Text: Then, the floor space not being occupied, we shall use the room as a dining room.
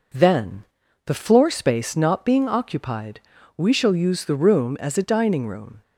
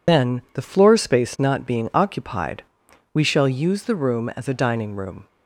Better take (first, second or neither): first